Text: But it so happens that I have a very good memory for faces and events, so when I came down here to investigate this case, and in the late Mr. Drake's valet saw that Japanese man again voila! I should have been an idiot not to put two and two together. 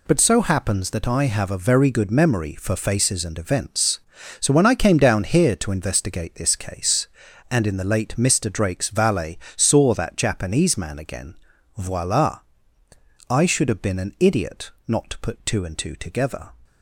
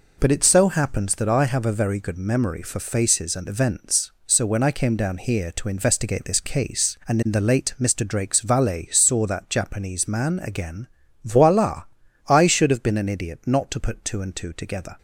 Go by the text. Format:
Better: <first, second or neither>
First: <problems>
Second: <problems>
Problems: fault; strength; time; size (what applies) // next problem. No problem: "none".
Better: second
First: skips "it"; at 0.1 s // pauses between "valet" and "saw"; slight; at 9.3 s; 0.18 s long // pauses between "again" and "voila"; at 11.3 s; 0.42 s long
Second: pauses between "again" and "voila"; at 10.8 s; 0.38 s long